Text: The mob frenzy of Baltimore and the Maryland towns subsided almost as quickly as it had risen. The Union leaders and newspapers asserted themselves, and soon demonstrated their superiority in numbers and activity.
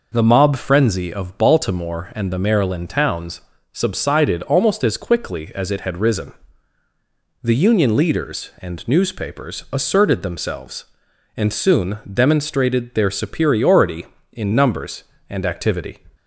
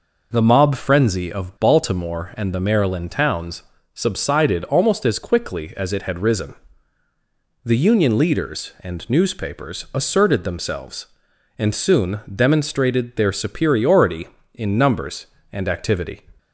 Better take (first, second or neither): neither